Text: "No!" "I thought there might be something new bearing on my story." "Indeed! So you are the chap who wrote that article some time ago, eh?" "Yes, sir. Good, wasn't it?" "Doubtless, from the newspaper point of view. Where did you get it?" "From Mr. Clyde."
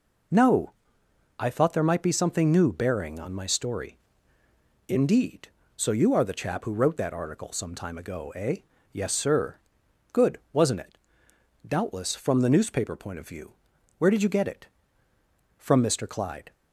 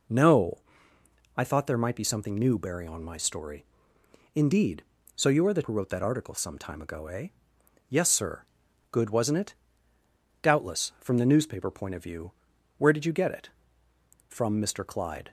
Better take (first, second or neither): first